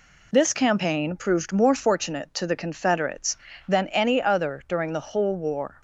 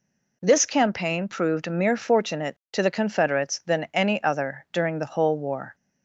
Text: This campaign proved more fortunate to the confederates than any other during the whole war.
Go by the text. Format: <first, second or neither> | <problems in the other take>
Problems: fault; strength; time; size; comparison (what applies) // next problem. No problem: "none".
first | says "mere" for "more"; at 1.6 s